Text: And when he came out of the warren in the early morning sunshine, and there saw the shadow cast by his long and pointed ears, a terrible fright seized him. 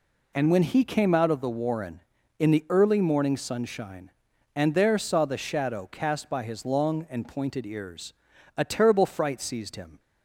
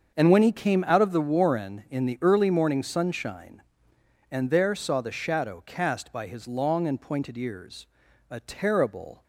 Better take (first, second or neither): first